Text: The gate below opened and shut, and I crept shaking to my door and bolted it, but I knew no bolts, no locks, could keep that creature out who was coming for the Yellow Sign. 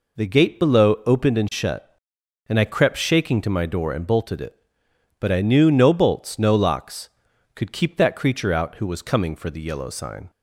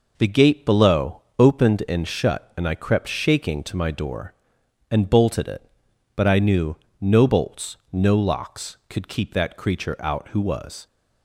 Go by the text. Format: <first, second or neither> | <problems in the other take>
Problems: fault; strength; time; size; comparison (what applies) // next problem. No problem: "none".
first | pauses between "knew" and "no"; slight; at 6.7 s; 0.24 s long // stops before "coming for the Yellow Sign"; at 10.8 s